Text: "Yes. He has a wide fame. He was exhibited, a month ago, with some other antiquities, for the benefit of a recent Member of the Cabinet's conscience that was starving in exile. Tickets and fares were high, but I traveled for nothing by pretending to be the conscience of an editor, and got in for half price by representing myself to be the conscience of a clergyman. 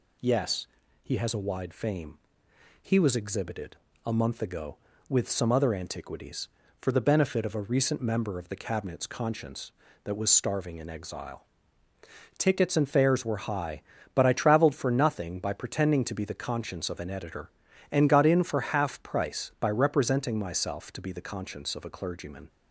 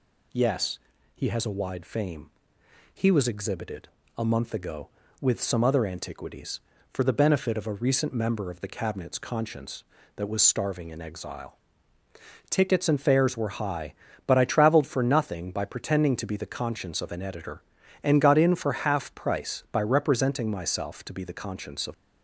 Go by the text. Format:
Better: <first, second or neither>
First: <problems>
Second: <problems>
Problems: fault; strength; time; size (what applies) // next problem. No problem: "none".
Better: first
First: none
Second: stops before "a clergyman"; at 21.9 s